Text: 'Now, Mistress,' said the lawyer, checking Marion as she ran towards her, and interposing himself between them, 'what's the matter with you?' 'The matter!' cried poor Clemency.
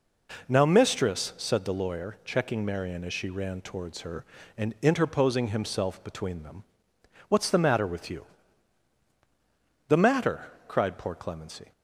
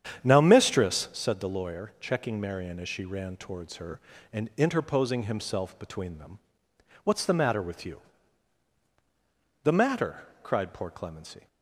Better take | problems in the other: first | starts louder than the rest; strong; until 1.2 s; 9 dB

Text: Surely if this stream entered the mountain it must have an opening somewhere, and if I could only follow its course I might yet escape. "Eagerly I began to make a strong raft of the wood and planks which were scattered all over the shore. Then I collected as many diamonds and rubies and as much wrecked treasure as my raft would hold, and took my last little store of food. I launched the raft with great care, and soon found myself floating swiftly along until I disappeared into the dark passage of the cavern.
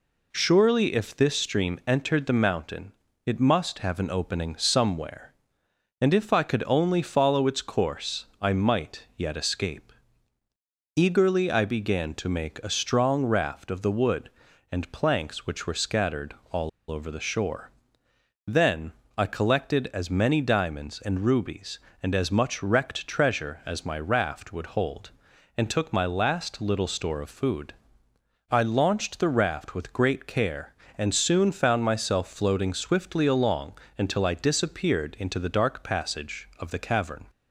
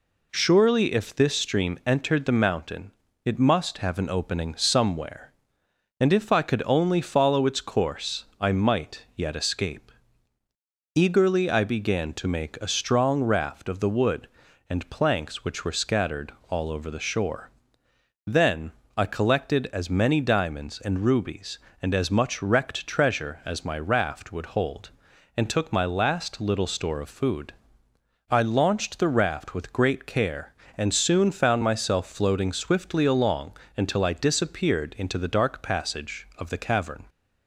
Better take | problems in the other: second | pauses between "mountain" and "it"; slight; at 2.9 s; 0.34 s long; slight in the second // pauses between "scattered" and "all"; slight; at 16.3 s; 0.16 s long; slight in the second // pauses between "all" and "over"; slight; at 16.6 s; 0.21 s long // pauses between "Then" and "I"; slight; at 18.9 s; 0.24 s long; slight in the second // pauses between "along" and "until"; slight; at 33.7 s; 0.22 s long; slight in the second

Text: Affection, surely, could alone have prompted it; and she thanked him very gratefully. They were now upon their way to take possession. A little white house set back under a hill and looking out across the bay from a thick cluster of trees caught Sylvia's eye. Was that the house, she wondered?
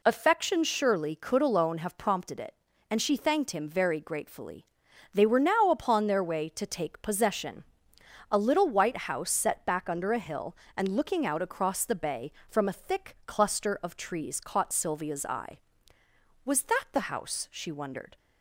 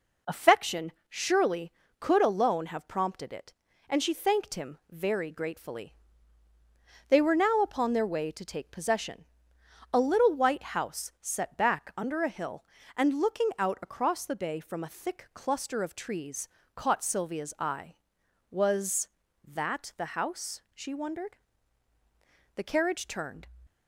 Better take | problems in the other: first | pauses between "trees" and "caught"; slight; at 16.4 s; 0.26 s long // goes on to say "The carriage turned"; noticeable; from 22.5 s on; 0.92 s long

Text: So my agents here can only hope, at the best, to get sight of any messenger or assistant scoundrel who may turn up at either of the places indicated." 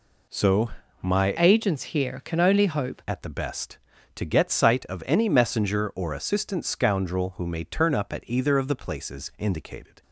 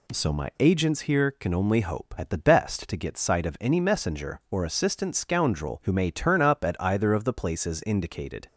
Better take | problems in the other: second | pauses between "So" and "my"; slight; at 0.6 s; 0.30 s long // changes voice from "agents" to "hope"; from 1.3 to 3.0 s; 1.7 s long

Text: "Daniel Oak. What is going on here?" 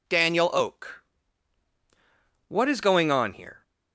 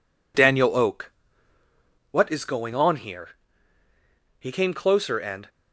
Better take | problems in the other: first | goes on to say "He came closer and"; noticeable; from 4.3 s on; 1.1 s long

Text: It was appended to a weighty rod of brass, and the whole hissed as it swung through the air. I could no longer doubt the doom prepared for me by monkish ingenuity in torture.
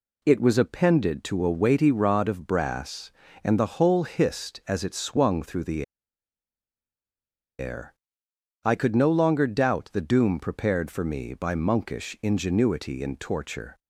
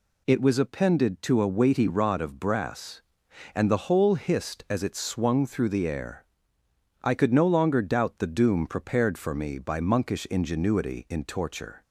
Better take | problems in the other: second | pauses between "the" and "air"; strong; at 5.8 s; 1.7 s long

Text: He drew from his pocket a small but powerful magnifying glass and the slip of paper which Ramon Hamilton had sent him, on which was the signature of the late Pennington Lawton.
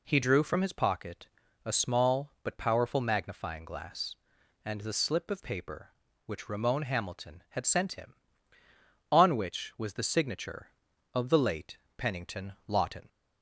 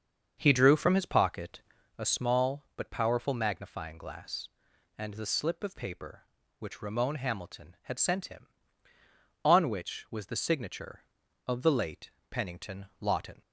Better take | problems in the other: first | starts louder than the rest; until 2.0 s; 7 dB // pauses between "pocket" and "a"; at 1.5 s; 0.38 s long; also in the first // pauses between "late" and "Pennington"; slight; at 12.1 s; 0.20 s long; slight in the first

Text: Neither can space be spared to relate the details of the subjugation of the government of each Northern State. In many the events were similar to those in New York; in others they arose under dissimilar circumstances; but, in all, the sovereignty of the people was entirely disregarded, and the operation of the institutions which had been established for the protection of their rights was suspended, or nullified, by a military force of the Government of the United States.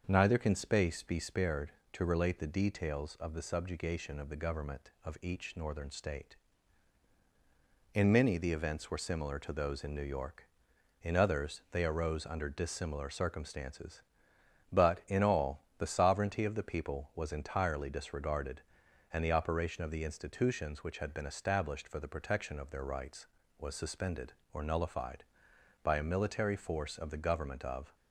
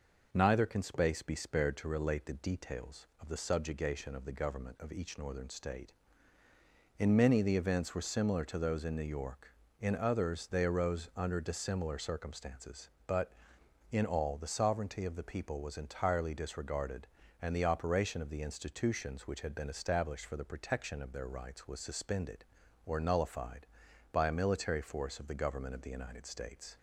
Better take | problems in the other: second | starts louder than the rest; until 1.0 s; 6.5 dB // stops before "the United States"; at 27.9 s

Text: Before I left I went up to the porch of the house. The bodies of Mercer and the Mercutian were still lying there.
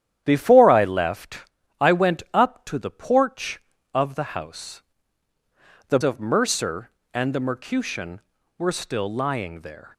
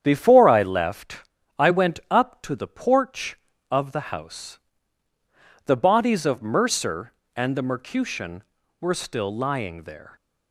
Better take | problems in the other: second | starts louder than the rest; strong; until 1.2 s; 10.5 dB; strong in the second // pauses between "left" and "I"; at 1.3 s; 0.42 s long; also in the second // skips "bodies"; at 6.0 s

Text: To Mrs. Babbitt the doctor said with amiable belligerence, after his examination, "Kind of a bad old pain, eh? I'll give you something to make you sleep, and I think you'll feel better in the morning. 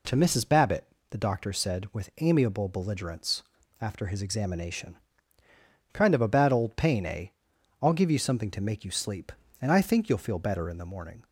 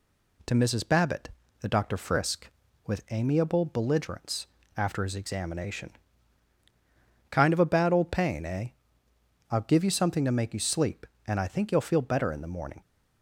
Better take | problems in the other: first | pauses between "Babbitt" and "the"; slight; at 1.2 s; 0.32 s long; slight in the first // says "frisk" for "said"; at 1.9 s

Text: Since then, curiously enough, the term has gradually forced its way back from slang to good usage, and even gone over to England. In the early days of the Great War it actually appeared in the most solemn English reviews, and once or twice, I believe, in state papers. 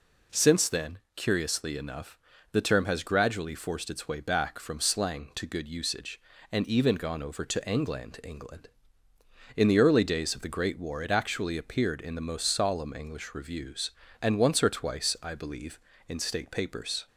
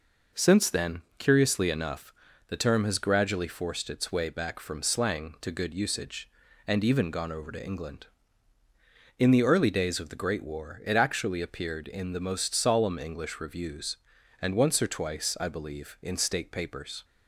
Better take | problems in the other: second | says "England" twice; at 8.2 s

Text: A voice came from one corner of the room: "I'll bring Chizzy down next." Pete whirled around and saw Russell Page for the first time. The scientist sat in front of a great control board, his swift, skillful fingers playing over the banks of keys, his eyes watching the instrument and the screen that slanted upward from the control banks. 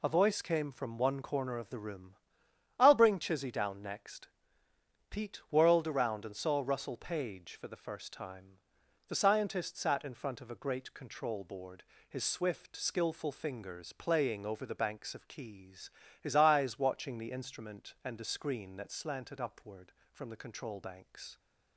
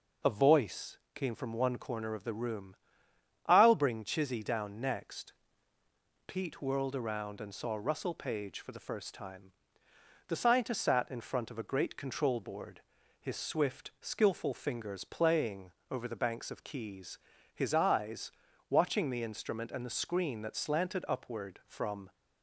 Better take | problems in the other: first | pauses between "voice" and "came"; slight; at 0.9 s; 0.18 s long // pauses between "playing" and "over"; slight; at 15.7 s; 0.18 s long // pauses between "eyes" and "watching"; at 18.3 s; 0.40 s long // stops before "the control banks"; at 22.1 s

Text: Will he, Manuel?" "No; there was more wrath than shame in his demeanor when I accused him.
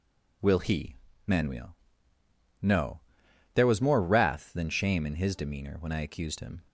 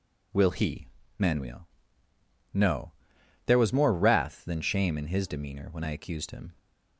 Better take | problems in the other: neither | none

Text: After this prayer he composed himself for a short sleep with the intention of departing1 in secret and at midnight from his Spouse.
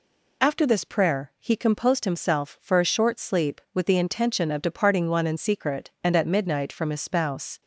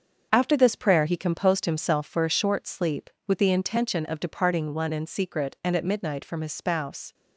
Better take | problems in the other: first | gets quieter; strong; throughout; 8 dB

